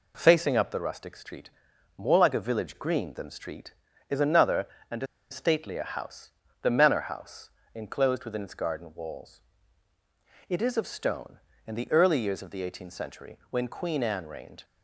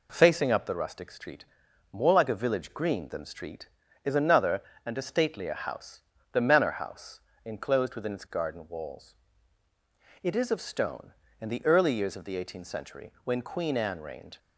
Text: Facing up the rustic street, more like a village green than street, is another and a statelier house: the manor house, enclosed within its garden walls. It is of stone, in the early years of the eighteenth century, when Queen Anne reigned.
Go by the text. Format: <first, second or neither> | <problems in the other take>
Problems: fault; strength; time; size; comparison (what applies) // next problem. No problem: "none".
second | pauses between "a" and "statelier"; slight; at 5.0 s; 0.24 s long